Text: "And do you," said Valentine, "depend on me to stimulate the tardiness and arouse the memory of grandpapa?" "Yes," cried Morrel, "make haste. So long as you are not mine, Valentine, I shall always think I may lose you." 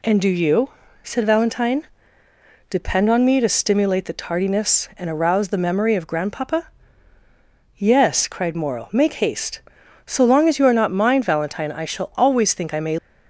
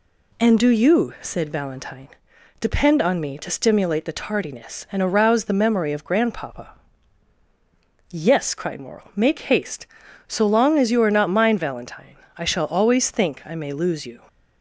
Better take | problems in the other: second | stops before "lose you"; at 12.9 s

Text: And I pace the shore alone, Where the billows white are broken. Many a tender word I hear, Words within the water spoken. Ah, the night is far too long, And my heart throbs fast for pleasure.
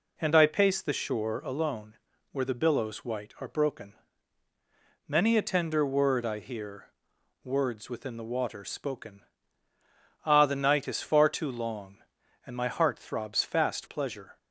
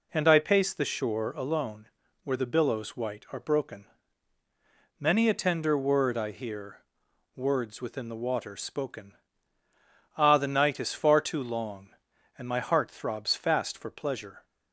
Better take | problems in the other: second | skips "for"; at 13.8 s

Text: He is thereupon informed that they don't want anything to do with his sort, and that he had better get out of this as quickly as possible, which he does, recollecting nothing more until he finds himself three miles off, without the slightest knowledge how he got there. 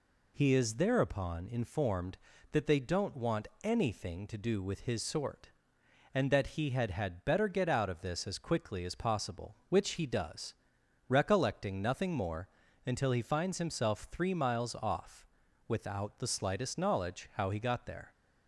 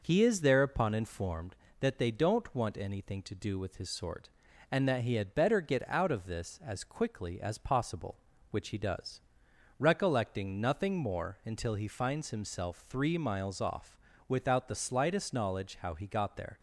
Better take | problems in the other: second | pauses between "want" and "anything"; slight; at 3.4 s; 0.16 s long // says "had" twice; at 6.9 s // pauses between "more" and "until"; slight; at 12.4 s; 0.36 s long

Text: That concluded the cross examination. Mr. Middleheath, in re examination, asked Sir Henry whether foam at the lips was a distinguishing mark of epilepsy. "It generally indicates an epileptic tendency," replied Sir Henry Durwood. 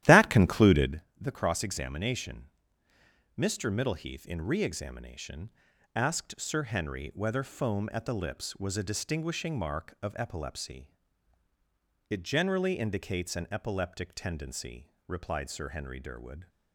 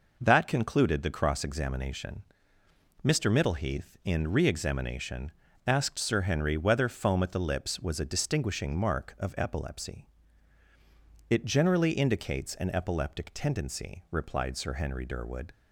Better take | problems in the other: second | starts louder than the rest; strong; until 1.0 s; 13 dB // pauses between "concluded" and "the"; slight; at 1.0 s; 0.18 s long

